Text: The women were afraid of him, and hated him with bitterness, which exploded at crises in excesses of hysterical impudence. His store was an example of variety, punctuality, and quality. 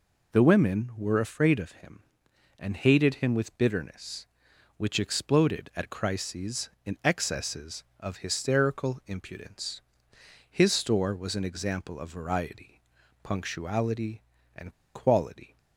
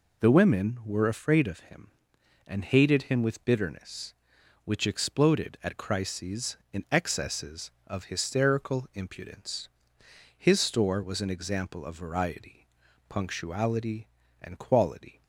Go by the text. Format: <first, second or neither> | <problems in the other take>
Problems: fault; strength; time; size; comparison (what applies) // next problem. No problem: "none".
second | pauses between "and" and "quality"; slight; at 14.7 s; 0.21 s long